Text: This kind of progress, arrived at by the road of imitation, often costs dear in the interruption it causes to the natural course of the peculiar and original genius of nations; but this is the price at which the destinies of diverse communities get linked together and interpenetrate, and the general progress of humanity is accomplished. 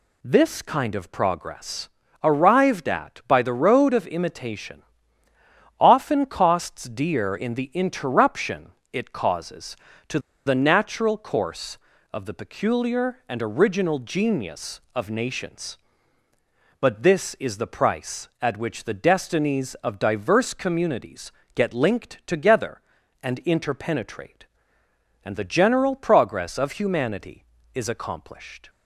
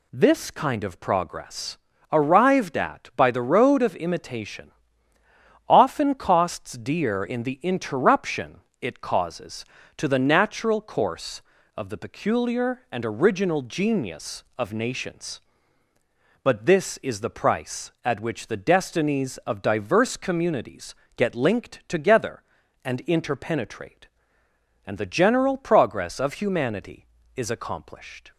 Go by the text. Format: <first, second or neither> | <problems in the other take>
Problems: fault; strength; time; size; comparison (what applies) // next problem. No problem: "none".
second | pauses between "interruption" and "it"; slight; at 8.7 s; 0.18 s long; slight in the second // pauses between "to" and "the"; slight; at 10.1 s; 0.27 s long // pauses between "communities" and "get"; slight; at 21.3 s; 0.24 s long; slight in the second